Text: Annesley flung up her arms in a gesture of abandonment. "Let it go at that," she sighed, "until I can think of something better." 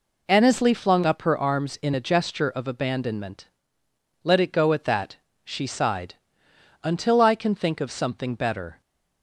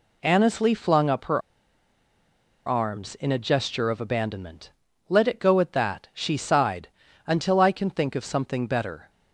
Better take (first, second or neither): first